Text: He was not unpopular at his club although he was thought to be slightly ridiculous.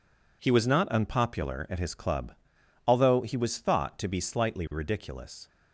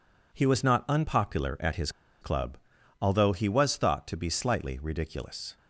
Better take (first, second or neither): first